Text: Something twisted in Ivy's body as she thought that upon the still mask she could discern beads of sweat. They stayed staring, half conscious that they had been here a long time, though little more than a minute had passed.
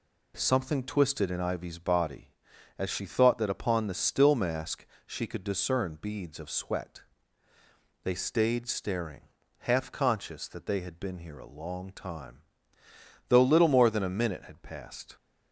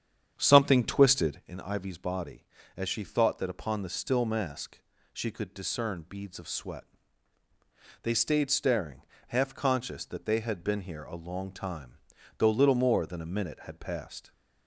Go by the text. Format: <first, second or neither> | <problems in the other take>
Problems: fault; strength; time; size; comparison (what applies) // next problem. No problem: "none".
first | starts louder than the rest; strong; until 1.5 s; 8.5 dB // pauses between "mask" and "she"; slight; at 4.8 s; 0.32 s long; slight in the first